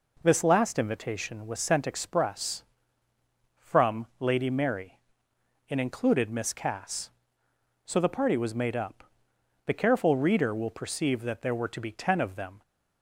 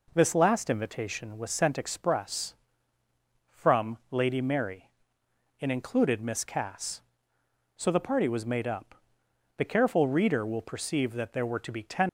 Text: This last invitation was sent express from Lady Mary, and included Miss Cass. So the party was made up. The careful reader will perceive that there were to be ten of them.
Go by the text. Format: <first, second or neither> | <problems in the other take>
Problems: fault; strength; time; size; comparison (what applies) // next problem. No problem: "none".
first | stops before "of them"; at 12.0 s